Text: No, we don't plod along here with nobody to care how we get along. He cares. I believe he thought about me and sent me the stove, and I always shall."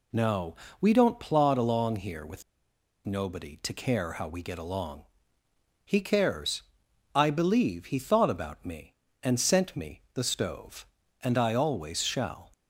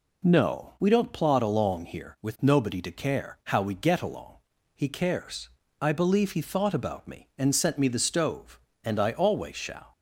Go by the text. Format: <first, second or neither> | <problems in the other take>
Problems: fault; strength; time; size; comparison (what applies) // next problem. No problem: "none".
second | pauses between "with" and "nobody"; noticeable; at 2.4 s; 0.63 s long